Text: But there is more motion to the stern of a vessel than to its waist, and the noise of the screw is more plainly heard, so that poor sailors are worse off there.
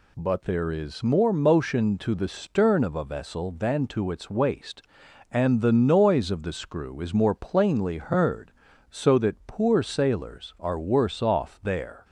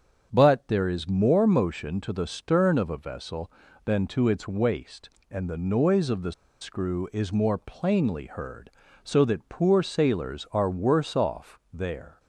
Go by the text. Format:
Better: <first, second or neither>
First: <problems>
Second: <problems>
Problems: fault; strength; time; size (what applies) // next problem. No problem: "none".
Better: first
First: none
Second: starts louder than the rest; strong; until 1.3 s; 7.5 dB // pauses between "the" and "screw"; slight; at 6.3 s; 0.28 s long